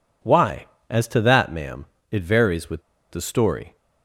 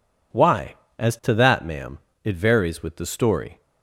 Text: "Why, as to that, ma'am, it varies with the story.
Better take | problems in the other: second | pauses between "with" and "the"; slight; at 2.8 s; 0.29 s long

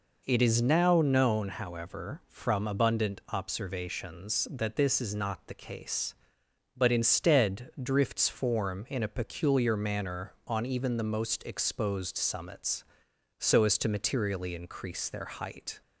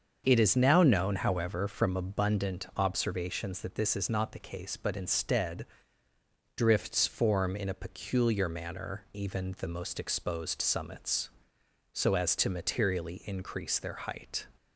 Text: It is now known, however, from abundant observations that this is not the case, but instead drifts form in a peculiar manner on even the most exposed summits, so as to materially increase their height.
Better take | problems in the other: first | starts louder than the rest; until 1.2 s; 6.5 dB // pauses between "instead" and "drifts"; noticeable; at 5.6 s; 0.90 s long // skips "on"; at 9.0 s

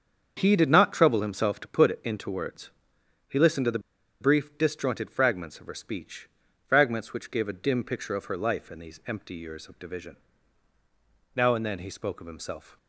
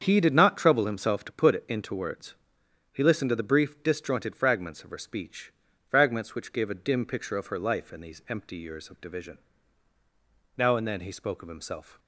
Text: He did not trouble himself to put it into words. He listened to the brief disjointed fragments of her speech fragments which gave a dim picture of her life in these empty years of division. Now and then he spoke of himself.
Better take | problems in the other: second | starts louder than the rest; strong; until 1.3 s; 7 dB; strong in the second // pauses between "the" and "brief"; at 3.7 s; 0.40 s long // pauses between "speech" and "fragments"; at 6.2 s; 0.38 s long; slight in the second

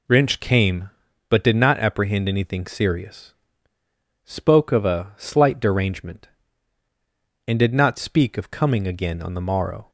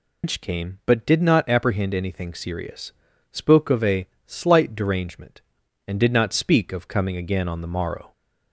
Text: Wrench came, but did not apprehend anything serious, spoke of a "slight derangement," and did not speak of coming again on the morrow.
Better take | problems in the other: first | loses the start of "Wrench"; at 0.2 s; 155 ms // pauses between "a" and "slight"; slight; at 4.0 s; 0.20 s long

